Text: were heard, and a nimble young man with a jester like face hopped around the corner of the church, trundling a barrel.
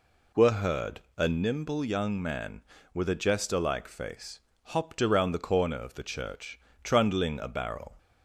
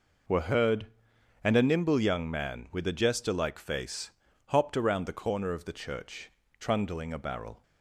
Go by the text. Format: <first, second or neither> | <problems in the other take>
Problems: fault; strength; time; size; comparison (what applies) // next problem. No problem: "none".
second | skips "and"; at 1.0 s // pauses between "face" and "hopped"; slight; at 4.3 s; 0.28 s long; slight in the second